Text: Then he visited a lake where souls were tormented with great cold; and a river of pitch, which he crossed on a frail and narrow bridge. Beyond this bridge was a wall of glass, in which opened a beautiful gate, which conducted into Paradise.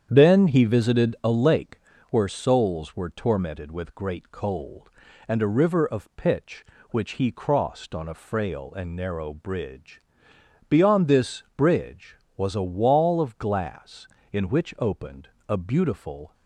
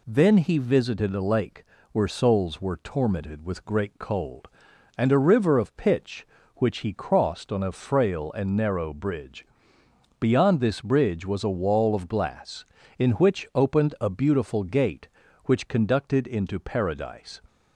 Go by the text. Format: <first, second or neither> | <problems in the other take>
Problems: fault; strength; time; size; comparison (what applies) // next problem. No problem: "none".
second | starts louder than the rest; strong; until 1.1 s; 8.5 dB // pauses between "lake" and "where"; slight; at 1.7 s; 0.32 s long; slight in the second // pauses between "opened" and "a"; slight; at 15.2 s; 0.20 s long // stops before "gate which conducted into Paradise"; at 16.3 s